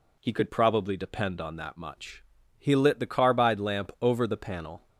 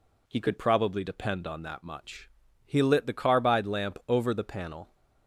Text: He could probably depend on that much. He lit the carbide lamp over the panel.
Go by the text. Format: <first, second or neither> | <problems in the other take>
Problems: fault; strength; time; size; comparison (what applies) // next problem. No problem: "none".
neither | none